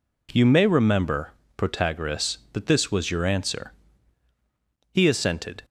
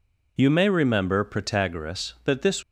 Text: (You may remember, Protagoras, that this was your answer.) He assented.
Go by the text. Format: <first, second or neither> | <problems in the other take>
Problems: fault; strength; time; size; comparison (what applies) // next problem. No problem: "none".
first | stops before "was your answer He assented"; at 2.6 s